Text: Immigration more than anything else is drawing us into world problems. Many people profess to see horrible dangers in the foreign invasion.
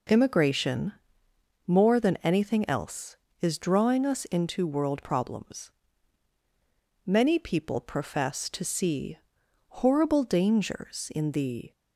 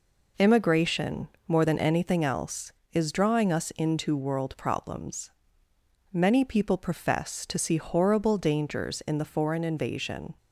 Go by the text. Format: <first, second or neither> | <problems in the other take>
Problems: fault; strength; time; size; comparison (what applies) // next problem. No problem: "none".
second | pauses between "Immigration" and "more"; noticeable; at 0.9 s; 0.72 s long; slight in the second // pauses between "see" and "horrible"; noticeable; at 9.1 s; 0.60 s long // stops before "foreign invasion"; at 11.7 s